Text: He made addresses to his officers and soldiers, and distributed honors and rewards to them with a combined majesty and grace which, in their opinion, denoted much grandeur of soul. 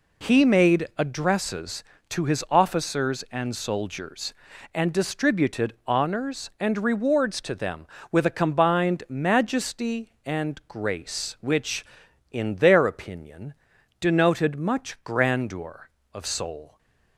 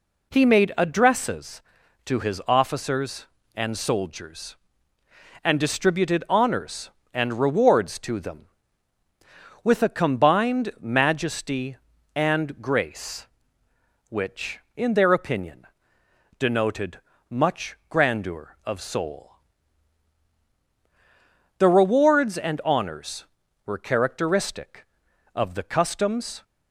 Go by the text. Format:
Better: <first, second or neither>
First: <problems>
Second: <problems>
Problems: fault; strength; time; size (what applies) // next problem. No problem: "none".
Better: first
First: none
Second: pauses between "denoted" and "much"; slight; at 16.9 s; 0.30 s long // goes on to say "The rewards and honors were characteristic of the customs"; strong; from 21.5 s on; 4.8 s long